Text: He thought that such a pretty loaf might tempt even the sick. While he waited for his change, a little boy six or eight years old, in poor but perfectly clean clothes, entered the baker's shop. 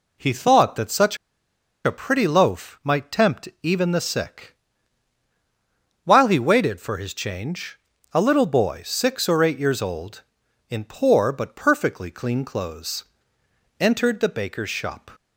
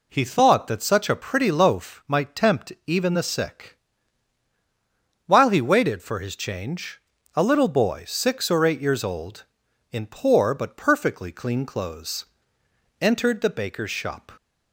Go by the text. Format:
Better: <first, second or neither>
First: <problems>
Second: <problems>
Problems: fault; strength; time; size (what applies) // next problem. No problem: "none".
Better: second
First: pauses between "such" and "a"; noticeable; at 1.1 s; 0.67 s long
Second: none